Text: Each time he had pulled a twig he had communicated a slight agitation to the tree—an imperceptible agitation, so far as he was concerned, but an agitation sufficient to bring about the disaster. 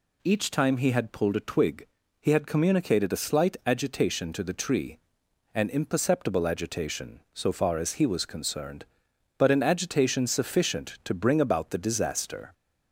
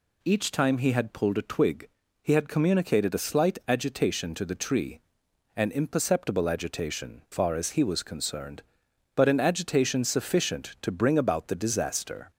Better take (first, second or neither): first